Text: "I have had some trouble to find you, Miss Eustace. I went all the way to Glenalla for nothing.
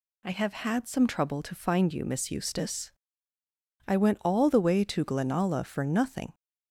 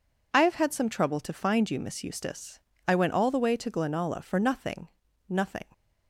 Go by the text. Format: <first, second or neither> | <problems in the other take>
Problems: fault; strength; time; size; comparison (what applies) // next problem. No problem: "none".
first | says "nothing" twice; at 5.2 s